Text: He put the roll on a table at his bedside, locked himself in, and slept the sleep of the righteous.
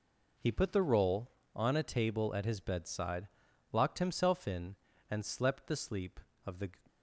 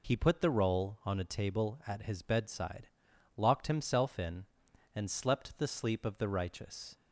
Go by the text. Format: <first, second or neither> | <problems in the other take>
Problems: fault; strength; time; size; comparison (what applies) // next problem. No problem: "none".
second | stops before "righteous"; at 6.8 s